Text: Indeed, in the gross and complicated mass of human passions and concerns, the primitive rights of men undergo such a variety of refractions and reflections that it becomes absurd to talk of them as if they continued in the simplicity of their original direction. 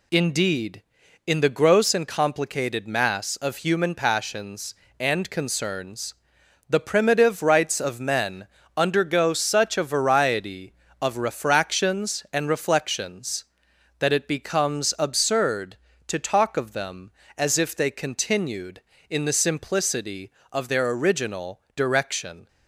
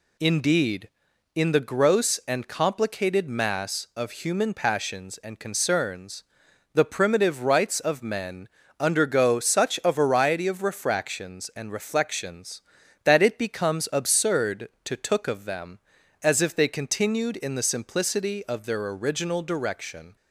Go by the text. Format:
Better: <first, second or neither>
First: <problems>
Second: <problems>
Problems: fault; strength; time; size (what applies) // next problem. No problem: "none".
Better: first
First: pauses between "men" and "undergo"; slight; at 8.4 s; 0.30 s long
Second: pauses between "men" and "undergo"; slight; at 8.4 s; 0.32 s long // says "took" for "talk"; at 14.9 s